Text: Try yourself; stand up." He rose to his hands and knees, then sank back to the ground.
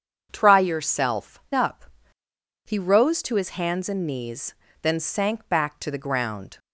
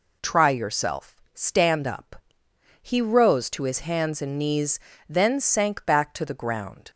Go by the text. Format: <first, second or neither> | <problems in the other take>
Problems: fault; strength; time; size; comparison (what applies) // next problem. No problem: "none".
second | starts louder than the rest; strong; until 1.3 s; 7.5 dB // skips "stand"; at 1.4 s